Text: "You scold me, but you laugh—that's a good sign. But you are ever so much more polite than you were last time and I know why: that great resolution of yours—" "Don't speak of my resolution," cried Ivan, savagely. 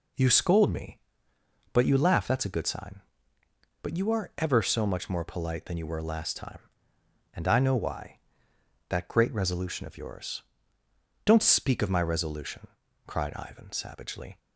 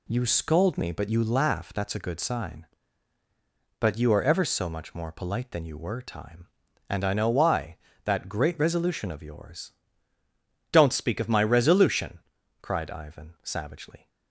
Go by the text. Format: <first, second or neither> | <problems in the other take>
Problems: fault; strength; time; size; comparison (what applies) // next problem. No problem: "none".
first | skips "last"; at 6.0 s